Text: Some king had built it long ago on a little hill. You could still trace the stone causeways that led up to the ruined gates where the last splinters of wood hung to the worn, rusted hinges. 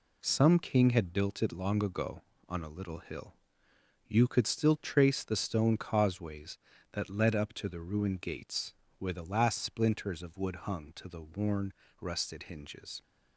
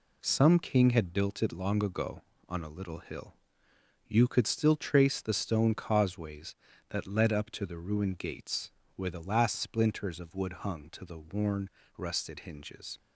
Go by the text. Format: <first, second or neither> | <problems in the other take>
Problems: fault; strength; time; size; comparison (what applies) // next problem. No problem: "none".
neither | pauses between "gates" and "where"; slight; the same in both